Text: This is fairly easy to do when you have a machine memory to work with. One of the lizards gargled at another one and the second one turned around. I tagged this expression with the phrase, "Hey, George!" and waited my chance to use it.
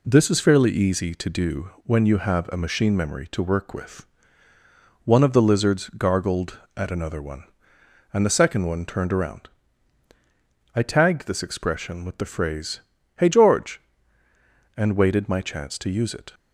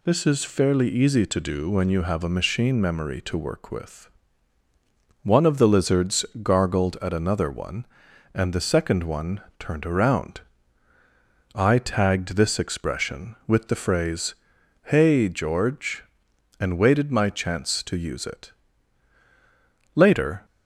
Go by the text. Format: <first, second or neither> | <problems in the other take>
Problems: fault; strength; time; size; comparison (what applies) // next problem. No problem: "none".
first | pauses between "lizards" and "gargled"; slight; at 6.2 s; 0.16 s long // pauses between "one" and "turned"; slight; at 9.4 s; 0.18 s long // goes on to say "Later"; from 19.9 s on; 0.52 s long